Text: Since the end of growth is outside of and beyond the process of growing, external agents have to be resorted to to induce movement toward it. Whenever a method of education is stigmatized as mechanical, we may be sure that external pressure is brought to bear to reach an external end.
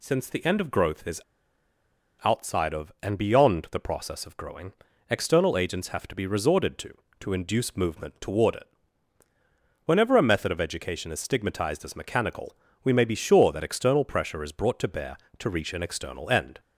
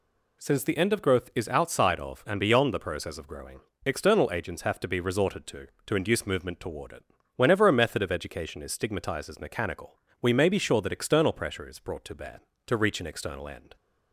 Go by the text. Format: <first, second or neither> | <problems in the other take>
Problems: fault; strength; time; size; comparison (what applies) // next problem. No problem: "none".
second | pauses between "is" and "outside"; at 1.2 s; 1.0 s long